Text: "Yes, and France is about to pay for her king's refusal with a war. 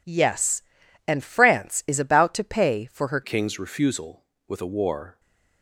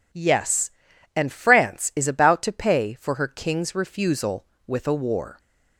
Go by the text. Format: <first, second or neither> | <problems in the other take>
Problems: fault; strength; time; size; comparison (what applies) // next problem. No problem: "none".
second | changes voice at "king's"; from 3.2 s on; 1.9 s long // stays silent after the last word; slight; from 5.1 s on; 0.5 s long